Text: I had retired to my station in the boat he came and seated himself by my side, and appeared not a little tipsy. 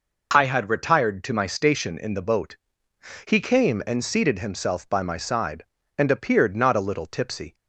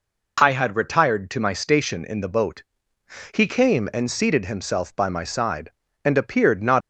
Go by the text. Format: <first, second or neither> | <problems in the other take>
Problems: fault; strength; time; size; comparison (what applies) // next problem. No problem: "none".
first | pauses between "boat" and "he"; noticeable; at 2.6 s; 0.72 s long; noticeable in the first // stops before "a little tipsy"; at 6.8 s